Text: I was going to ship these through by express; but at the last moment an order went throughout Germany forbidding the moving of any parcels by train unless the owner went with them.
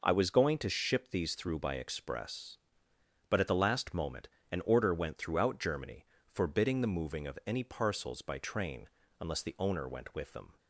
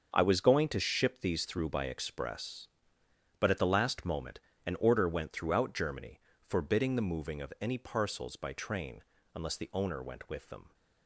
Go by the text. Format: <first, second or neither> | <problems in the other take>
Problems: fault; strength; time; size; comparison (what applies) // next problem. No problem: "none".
first | gets quieter; strong; throughout; 11 dB // pauses between "moment" and "an"; slight; at 4.4 s; 0.23 s long; slight in the first // pauses between "Germany" and "forbidding"; slight; at 6.1 s; 0.26 s long; slight in the first // pauses between "train" and "unless"; slight; at 9.0 s; 0.32 s long; slight in the first